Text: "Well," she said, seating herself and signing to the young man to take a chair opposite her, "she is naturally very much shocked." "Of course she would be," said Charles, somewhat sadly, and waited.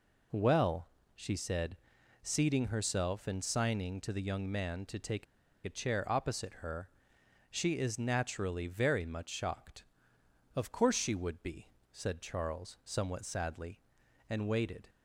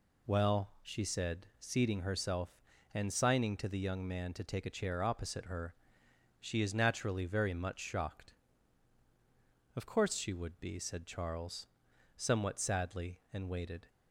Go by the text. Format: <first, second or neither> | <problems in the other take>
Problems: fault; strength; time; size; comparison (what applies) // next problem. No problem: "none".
second | pauses between "take" and "a"; at 5.2 s; 0.40 s long